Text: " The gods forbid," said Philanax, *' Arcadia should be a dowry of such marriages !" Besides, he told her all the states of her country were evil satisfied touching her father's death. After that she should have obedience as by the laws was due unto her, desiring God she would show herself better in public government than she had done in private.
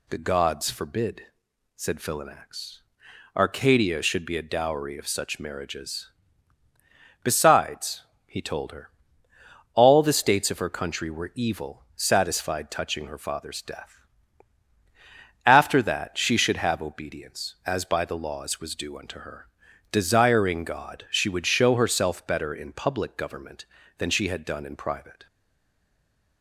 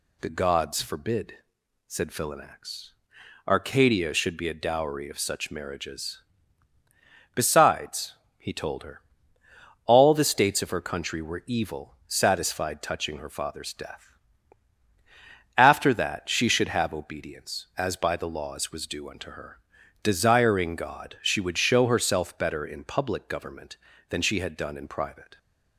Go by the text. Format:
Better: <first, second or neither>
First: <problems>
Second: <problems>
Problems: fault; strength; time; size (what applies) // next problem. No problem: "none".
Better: second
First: pauses between "her" and "all"; noticeable; at 8.8 s; 0.86 s long // stays silent after the last word; from 25.2 s on; 1.2 s long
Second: pauses between "her" and "all"; noticeable; at 8.9 s; 0.86 s long